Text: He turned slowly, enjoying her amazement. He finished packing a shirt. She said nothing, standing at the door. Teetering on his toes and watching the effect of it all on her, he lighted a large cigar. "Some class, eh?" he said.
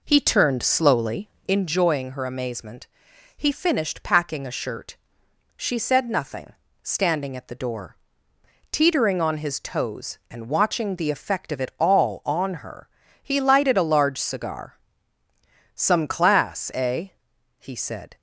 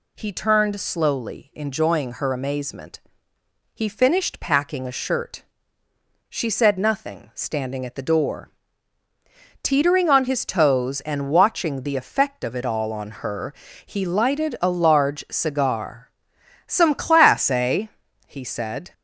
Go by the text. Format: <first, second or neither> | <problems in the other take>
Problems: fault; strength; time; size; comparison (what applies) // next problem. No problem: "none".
second | starts louder than the rest; noticeable; until 1.6 s; 4.5 dB